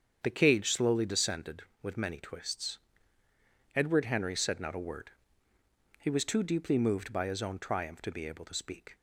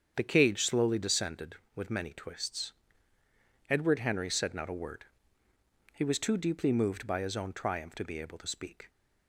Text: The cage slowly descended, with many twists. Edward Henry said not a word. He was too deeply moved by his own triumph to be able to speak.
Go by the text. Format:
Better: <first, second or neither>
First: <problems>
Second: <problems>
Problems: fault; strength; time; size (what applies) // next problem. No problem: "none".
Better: neither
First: starts louder than the rest; strong; until 1.2 s; 7.5 dB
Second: starts louder than the rest; strong; until 1.1 s; 7.5 dB